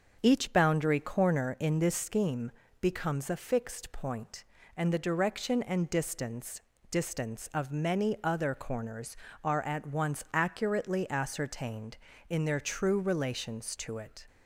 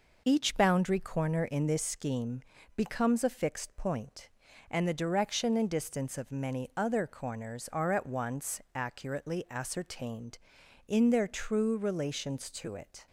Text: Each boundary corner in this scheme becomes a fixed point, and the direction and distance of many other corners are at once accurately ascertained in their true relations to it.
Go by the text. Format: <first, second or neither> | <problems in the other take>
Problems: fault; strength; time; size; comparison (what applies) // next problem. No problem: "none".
second | starts louder than the rest; until 1.2 s; 6.5 dB // pauses between "scheme" and "becomes"; slight; at 2.5 s; 0.30 s long; slight in the second // says "distance" twice; at 6.9 s